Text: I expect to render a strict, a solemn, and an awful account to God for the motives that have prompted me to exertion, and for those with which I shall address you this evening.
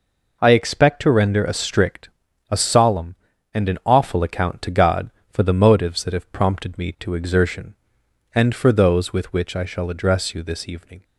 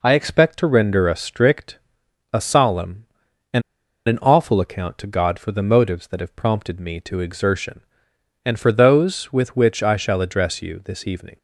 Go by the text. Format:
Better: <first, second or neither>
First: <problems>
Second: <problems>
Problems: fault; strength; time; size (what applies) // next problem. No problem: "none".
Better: first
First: none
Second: pauses between "and" and "an"; at 3.6 s; 0.45 s long